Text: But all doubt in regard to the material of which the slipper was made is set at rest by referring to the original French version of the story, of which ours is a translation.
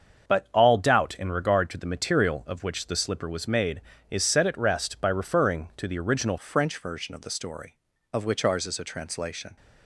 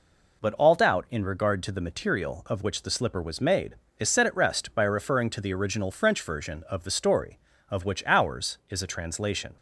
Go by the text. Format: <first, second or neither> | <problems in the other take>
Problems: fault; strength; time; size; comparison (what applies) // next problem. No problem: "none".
second | starts louder than the rest; until 1.3 s; 7 dB // changes voice at "French"; from 6.3 s on; 3.2 s long